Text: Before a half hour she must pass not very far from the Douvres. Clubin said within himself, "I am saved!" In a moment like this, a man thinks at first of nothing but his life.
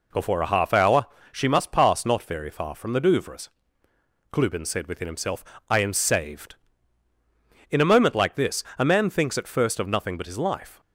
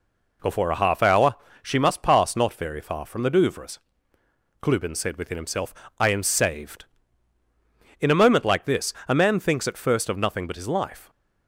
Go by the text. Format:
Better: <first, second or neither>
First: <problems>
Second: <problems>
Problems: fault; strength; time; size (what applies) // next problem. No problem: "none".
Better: neither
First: pauses between "hour" and "she"; slight; at 1.0 s; 0.27 s long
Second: pauses between "hour" and "she"; slight; at 1.3 s; 0.28 s long